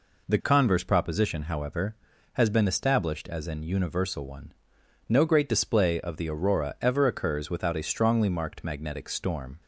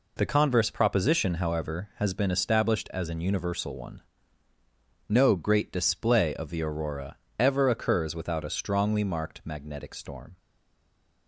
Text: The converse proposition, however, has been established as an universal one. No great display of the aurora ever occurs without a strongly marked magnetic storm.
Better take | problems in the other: first | pauses between "aurora" and "ever"; slight; at 7.1 s; 0.22 s long // stays silent after the last word; slight; from 10.3 s on; 0.9 s long

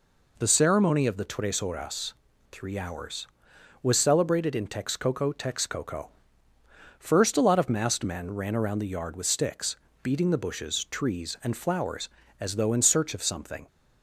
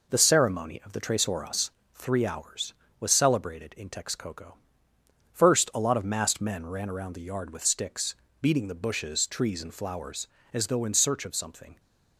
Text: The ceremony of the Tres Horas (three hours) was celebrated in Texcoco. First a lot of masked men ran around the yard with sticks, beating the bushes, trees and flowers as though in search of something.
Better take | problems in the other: second | says "Texcoco" twice; at 5.3 s

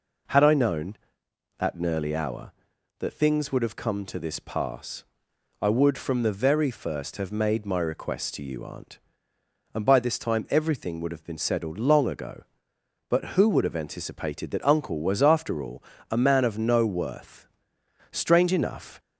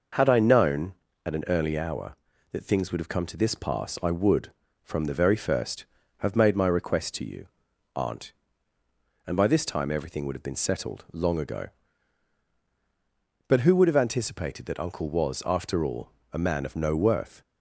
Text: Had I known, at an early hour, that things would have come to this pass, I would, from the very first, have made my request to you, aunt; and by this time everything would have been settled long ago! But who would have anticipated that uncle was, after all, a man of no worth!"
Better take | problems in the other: second | goes on to say "Strange enough"; noticeable; from 18.1 s on; 0.88 s long

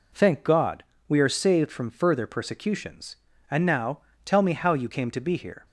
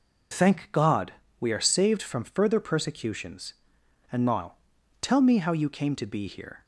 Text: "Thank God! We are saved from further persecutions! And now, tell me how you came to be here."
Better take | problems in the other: neither | none

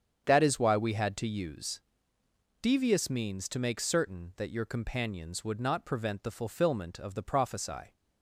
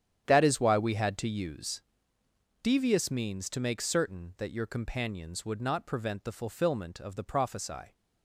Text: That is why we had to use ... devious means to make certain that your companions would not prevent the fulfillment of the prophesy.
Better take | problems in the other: first | gets quieter; strong; throughout; 13 dB // starts louder than the rest; strong; until 1.3 s; 9.5 dB; strong in the first

